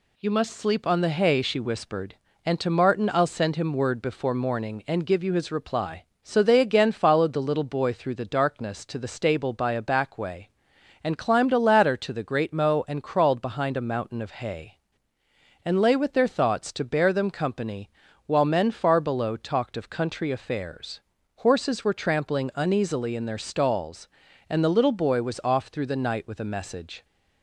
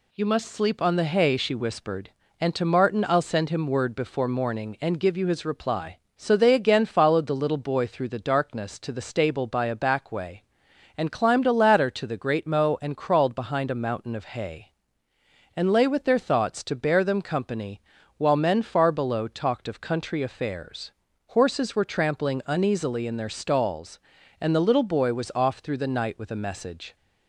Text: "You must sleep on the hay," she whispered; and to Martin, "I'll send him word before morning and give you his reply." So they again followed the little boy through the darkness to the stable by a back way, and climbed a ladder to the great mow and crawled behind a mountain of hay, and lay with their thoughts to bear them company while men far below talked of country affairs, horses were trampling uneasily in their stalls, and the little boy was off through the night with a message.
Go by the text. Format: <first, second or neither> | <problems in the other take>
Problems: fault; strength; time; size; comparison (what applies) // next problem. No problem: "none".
neither | pauses between "company" and "while"; the same in both